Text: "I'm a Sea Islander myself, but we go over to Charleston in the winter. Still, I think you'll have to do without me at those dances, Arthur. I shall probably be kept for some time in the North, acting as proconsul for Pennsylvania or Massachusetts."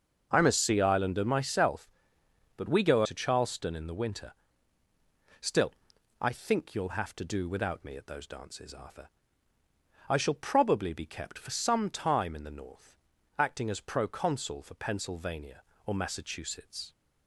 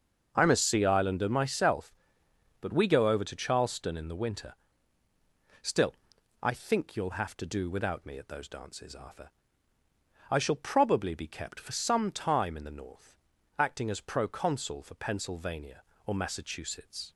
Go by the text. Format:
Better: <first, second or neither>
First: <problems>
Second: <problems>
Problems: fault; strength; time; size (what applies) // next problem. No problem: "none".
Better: second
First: starts louder than the rest; until 1.3 s; 6.5 dB // skips "over"; at 3.0 s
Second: starts louder than the rest; until 1.3 s; 6.5 dB